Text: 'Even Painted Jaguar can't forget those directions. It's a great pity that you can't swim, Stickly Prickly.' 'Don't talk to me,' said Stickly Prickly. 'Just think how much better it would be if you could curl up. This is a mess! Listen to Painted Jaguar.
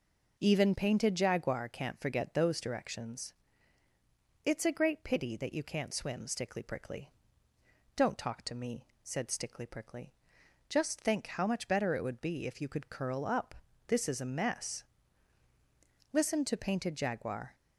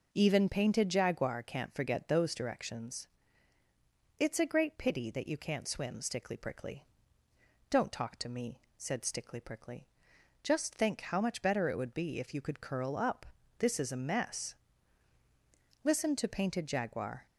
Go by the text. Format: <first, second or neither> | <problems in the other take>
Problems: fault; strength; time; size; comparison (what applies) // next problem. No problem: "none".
neither | none